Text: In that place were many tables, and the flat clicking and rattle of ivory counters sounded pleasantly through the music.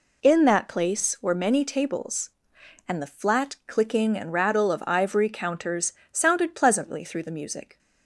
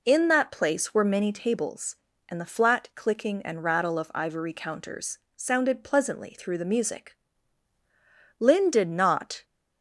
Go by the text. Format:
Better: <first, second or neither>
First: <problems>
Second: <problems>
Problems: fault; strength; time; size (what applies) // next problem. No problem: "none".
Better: first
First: pauses between "counters" and "sounded"; slight; at 5.9 s; 0.18 s long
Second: pauses between "counters" and "sounded"; slight; at 5.1 s; 0.18 s long // goes on to say "Lin did not"; noticeable; from 8.3 s on; 1.0 s long